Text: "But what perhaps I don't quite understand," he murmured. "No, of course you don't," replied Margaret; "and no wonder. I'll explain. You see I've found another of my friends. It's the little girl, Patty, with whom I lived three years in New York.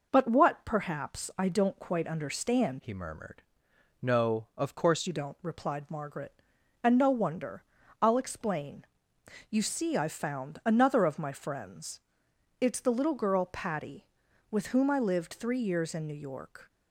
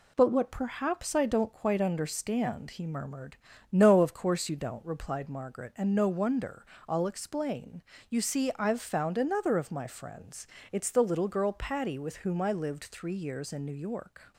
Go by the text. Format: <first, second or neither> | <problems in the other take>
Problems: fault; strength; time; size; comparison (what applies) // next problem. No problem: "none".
second | changes voice from "he" to "course"; from 2.7 to 5.0 s; 2.3 s long